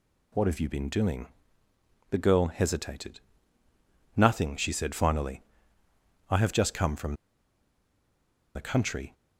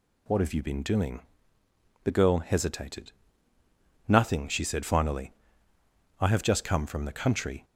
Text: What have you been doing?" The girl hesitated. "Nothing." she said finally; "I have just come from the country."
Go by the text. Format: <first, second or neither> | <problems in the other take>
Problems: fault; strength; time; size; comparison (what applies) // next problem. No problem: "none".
second | pauses between "from" and "the"; strong; at 7.1 s; 1.4 s long